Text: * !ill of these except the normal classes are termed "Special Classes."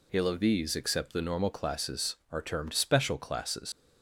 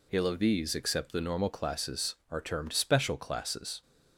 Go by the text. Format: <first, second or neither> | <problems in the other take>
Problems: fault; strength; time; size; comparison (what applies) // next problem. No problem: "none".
second | leaves "Classes" unfinished; at 3.7 s; 100 ms